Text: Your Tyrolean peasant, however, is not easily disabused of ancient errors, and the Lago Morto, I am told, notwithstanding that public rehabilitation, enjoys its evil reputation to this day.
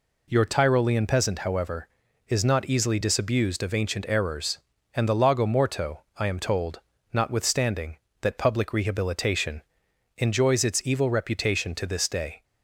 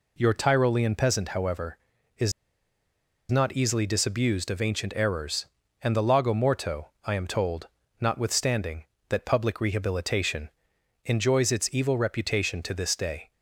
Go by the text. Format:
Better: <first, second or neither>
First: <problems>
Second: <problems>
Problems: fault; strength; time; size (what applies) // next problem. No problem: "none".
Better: first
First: none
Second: pauses between "is" and "not"; at 2.3 s; 0.98 s long